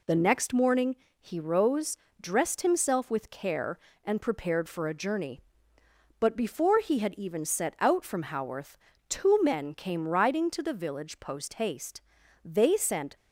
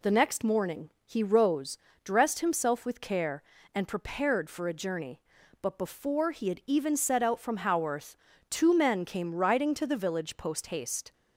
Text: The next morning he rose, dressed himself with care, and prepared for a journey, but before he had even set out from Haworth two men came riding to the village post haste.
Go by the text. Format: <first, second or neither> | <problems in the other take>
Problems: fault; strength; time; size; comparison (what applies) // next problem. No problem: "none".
second | pauses between "morning" and "he"; slight; at 0.9 s; 0.26 s long; slight in the second // pauses between "Haworth" and "two"; slight; at 8.7 s; 0.30 s long; slight in the second // goes on to say "They sent"; noticeable; from 12.4 s on; 0.72 s long